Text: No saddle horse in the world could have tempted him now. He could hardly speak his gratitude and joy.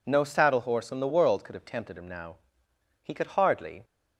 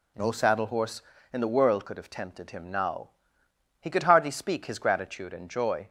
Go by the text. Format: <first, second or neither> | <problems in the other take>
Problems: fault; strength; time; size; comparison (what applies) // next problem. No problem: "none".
second | stops before "speak his gratitude and joy"; at 3.8 s